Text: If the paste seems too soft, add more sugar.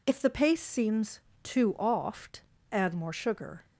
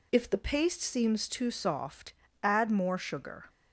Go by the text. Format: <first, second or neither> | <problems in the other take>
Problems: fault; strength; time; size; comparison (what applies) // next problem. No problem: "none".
second | pauses between "seems" and "too"; slight; at 1.2 s; 0.22 s long // says "oft" for "soft"; at 1.7 s